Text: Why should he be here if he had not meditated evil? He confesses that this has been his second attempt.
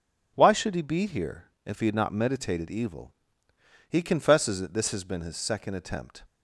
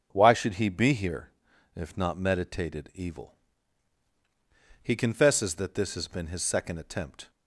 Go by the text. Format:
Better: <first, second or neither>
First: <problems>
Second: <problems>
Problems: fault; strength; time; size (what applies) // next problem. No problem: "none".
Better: first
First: pauses between "here" and "if"; slight; at 1.4 s; 0.20 s long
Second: starts louder than the rest; until 1.1 s; 6.5 dB // pauses between "here" and "if"; noticeable; at 1.3 s; 0.46 s long // skips "he had"; at 1.9 s